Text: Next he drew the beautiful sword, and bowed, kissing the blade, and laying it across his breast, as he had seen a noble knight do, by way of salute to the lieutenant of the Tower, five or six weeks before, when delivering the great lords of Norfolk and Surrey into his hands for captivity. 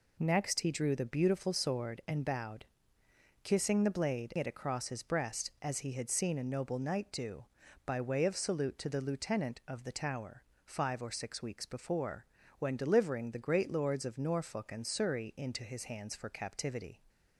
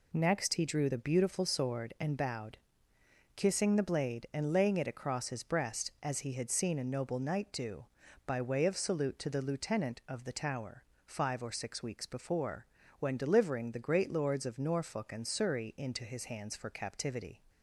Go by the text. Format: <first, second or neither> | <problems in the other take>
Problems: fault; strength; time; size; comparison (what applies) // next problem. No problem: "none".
second | skips "and laying"; at 4.3 s